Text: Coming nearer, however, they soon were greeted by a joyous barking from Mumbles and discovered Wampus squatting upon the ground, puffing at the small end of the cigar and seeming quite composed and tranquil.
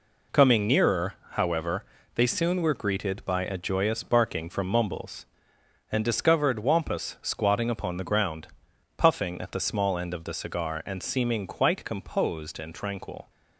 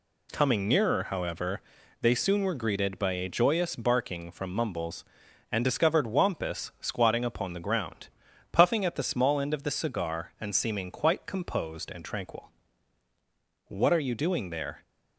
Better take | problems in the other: first | goes on to say "What are you doing there"; noticeable; from 13.6 s on; 1.1 s long

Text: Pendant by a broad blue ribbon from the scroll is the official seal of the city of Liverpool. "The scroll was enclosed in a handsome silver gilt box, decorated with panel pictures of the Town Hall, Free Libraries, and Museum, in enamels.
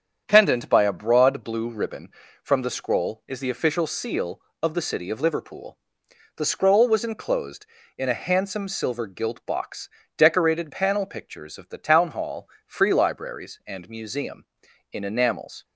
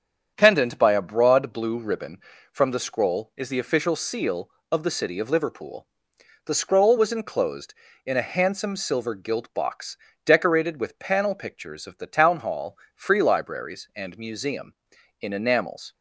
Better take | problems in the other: second | starts louder than the rest; strong; until 1.2 s; 8 dB; strong in the second // skips "with"; at 10.7 s

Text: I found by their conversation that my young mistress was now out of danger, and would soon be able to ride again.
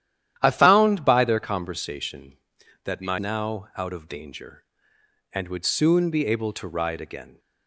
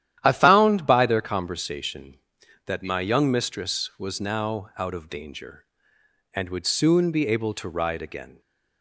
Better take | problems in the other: second | starts louder than the rest; strong; until 1.3 s; 11.5 dB; strong in the second // skips "young mistress was"; at 3.1 s

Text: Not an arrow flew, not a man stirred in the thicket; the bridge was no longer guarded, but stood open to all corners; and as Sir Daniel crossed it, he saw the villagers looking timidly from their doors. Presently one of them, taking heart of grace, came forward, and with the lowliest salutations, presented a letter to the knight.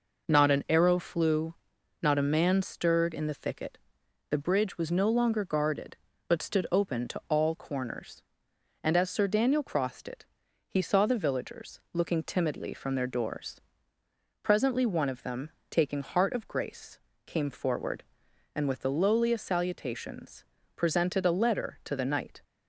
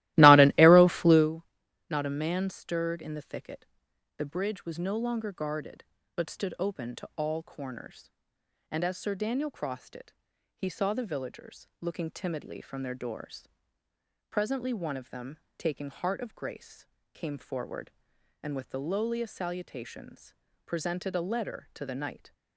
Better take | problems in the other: first | starts louder than the rest; strong; until 1.3 s; 17.5 dB

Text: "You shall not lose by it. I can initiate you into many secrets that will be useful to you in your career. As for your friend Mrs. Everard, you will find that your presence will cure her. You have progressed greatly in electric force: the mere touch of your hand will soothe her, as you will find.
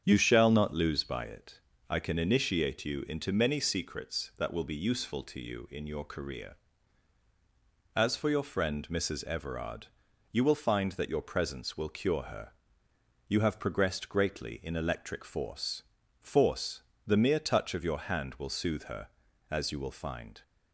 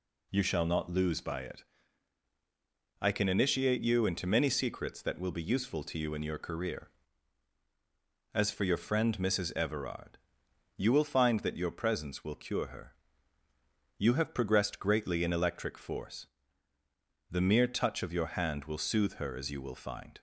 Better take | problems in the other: second | starts louder than the rest; strong; until 1.0 s; 8 dB // says "force" twice; at 16.1 s

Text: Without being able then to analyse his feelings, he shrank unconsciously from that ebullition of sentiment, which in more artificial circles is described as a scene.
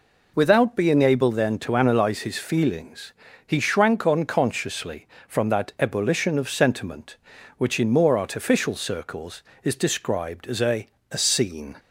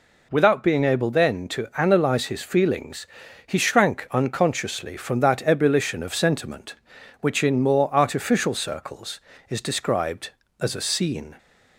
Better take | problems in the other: second | says "a" twice; at 11.1 s

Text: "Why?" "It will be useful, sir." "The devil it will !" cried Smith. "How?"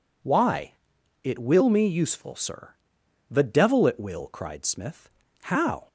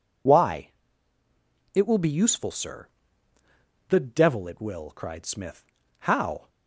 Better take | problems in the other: second | says "me" for "be"; at 1.6 s

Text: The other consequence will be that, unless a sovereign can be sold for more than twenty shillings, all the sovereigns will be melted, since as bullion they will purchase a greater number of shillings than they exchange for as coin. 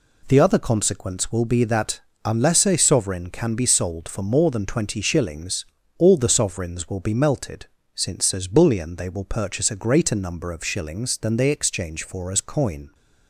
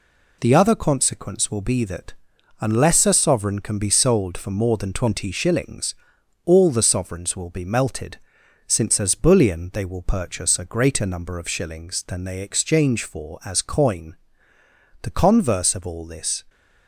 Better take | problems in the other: first | goes on to say "The converse of all this"; from 15.0 s on; 1.4 s long

